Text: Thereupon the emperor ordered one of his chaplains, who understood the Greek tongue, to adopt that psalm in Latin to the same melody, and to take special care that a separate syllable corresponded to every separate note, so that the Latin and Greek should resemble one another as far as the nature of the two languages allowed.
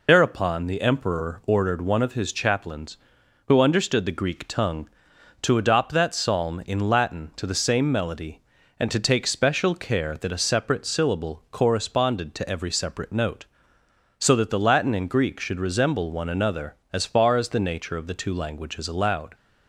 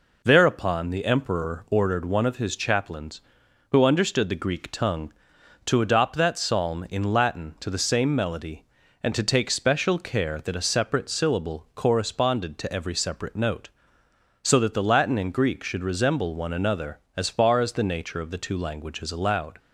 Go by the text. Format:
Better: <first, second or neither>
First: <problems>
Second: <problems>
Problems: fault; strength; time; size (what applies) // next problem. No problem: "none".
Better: second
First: loses the start of "Thereupon"; at 0.0 s; 80 ms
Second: none